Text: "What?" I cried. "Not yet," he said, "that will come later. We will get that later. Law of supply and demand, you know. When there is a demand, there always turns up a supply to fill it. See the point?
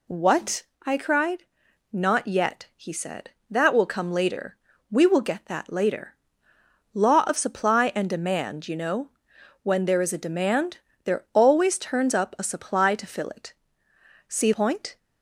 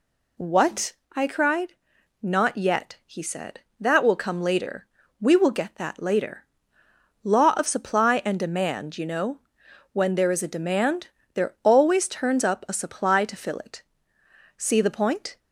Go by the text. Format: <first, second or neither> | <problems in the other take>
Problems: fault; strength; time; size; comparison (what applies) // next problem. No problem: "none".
second | skips "the"; at 14.5 s